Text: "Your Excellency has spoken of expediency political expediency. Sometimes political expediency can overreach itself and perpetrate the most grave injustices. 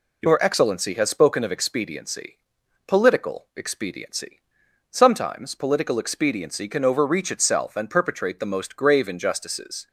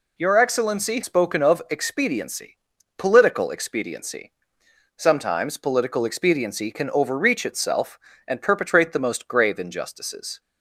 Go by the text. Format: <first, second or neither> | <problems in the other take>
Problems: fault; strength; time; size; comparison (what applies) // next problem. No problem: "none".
first | skips "has"; at 1.0 s // pauses between "expediency" and "political"; at 2.5 s; 0.42 s long; noticeable in the first